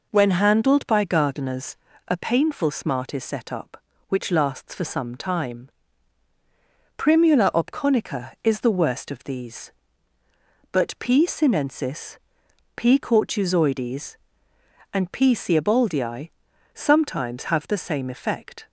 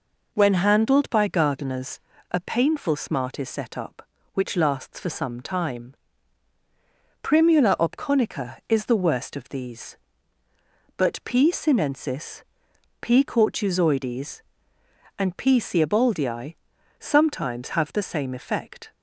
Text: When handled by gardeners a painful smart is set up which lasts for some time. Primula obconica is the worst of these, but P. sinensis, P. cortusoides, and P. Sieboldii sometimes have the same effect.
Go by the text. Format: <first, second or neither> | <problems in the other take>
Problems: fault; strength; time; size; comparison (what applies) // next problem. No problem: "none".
neither | pauses between "gardeners" and "a"; slight; the same in both // pauses between "Sieboldii" and "sometimes"; the same in both